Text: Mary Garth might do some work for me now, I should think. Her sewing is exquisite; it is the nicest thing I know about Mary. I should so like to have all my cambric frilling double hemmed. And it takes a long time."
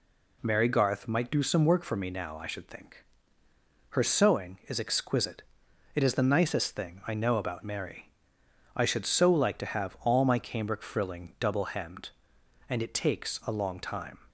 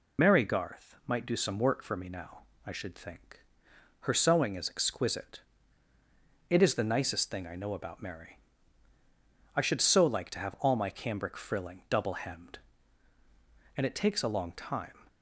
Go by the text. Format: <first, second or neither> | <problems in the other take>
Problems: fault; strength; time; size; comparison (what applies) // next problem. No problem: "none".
first | loses the start of "Mary"; at 0.1 s; 35 ms